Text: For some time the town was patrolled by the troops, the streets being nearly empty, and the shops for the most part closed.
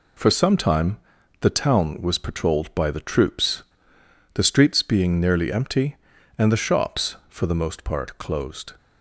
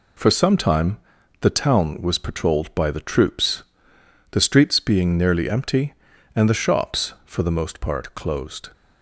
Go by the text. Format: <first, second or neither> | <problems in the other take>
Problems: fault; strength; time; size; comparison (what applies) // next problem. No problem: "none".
neither | pauses between "time" and "the"; the same in both